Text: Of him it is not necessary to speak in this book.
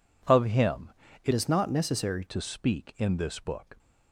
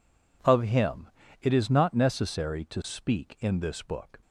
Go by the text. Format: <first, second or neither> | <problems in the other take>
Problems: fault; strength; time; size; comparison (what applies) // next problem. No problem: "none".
second | pauses between "him" and "it"; slight; at 0.9 s; 0.34 s long; slight in the second // changes voice from "is" to "necessary"; from 1.3 to 2.2 s; 0.9 s long